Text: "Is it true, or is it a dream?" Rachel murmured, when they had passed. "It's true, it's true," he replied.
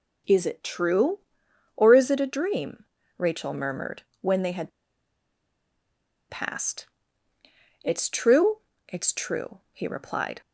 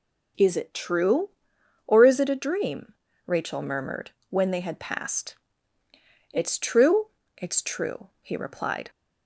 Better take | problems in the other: second | pauses between "had" and "passed"; strong; at 4.7 s; 1.6 s long

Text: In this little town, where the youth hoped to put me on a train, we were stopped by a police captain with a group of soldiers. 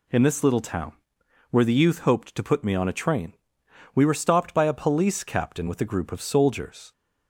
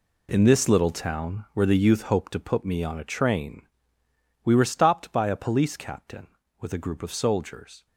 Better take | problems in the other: first | gets quieter; strong; throughout; 11.5 dB

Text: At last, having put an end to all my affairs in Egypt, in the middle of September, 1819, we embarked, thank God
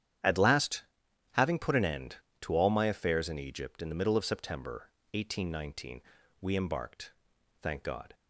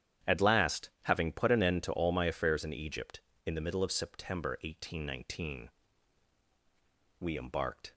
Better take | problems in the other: first | starts louder than the rest; strong; until 1.4 s; 9.5 dB; strong in the first // stops before "thank God"; at 7.9 s

